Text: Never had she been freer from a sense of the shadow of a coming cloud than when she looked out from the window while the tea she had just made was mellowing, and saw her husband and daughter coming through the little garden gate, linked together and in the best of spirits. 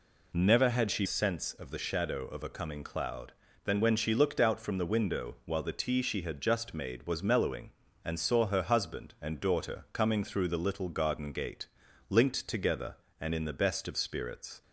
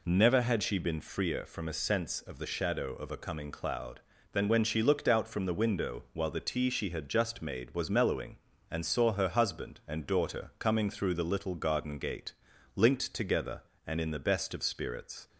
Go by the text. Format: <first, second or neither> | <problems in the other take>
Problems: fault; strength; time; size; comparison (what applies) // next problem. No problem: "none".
second | skips "been freer from a"; at 1.0 s